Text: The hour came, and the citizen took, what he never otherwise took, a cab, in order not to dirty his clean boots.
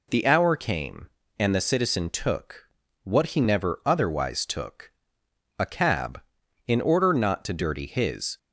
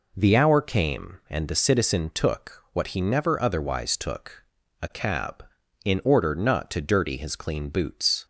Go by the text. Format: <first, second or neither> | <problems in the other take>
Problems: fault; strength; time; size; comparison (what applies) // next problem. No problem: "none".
second | stops before "clean boots"; at 8.3 s